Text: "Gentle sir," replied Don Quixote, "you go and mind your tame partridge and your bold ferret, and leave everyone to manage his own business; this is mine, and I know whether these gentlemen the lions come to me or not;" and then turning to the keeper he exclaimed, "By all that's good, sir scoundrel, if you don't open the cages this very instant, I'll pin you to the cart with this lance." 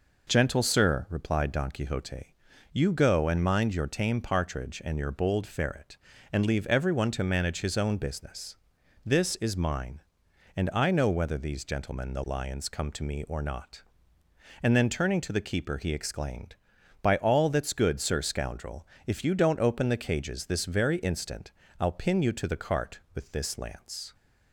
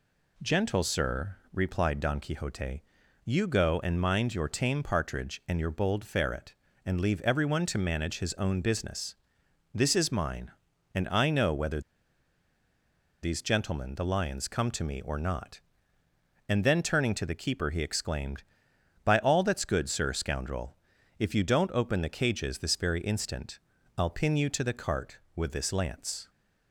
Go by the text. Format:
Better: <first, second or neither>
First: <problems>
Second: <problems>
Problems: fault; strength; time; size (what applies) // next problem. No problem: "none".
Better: first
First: none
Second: pauses between "whether" and "these"; strong; at 11.8 s; 1.4 s long